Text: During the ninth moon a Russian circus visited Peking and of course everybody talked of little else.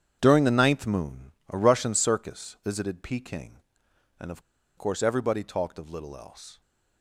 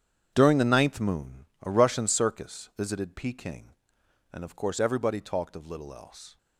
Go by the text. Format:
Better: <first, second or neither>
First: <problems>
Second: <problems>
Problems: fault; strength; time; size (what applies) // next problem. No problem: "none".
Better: second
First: starts louder than the rest; strong; until 1.2 s; 8.5 dB // pauses between "moon" and "a"; slight; at 1.3 s; 0.18 s long // pauses between "of" and "course"; at 4.4 s; 0.36 s long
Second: starts louder than the rest; strong; until 1.3 s; 8.5 dB // pauses between "moon" and "a"; slight; at 1.4 s; 0.17 s long